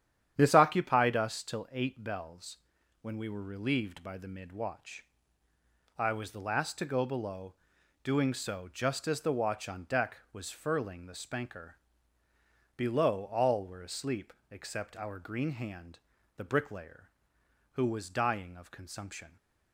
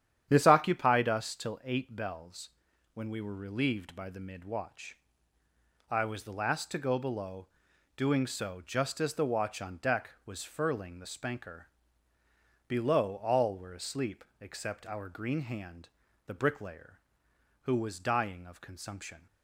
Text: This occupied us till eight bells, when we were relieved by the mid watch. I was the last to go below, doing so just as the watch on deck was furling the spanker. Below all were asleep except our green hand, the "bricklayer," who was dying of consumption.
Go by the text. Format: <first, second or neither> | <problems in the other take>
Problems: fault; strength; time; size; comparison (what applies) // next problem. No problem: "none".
neither | starts louder than the rest; strong; the same in both // pauses between "asleep" and "except"; slight; the same in both